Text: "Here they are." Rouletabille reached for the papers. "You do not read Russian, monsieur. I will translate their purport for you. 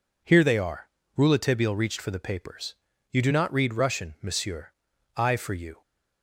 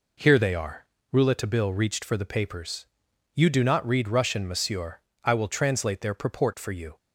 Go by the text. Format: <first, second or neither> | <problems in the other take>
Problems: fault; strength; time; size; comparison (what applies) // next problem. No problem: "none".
second | skips "will translate their purport"; at 5.3 s